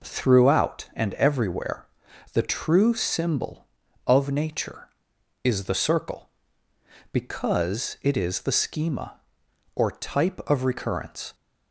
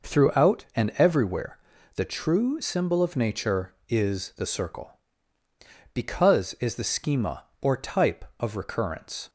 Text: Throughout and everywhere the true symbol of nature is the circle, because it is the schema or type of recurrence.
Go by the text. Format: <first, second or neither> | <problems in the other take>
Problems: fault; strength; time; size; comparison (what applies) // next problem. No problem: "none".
first | pauses between "everywhere" and "the"; at 1.5 s; 0.38 s long; noticeable in the first // skips "it"; at 6.5 s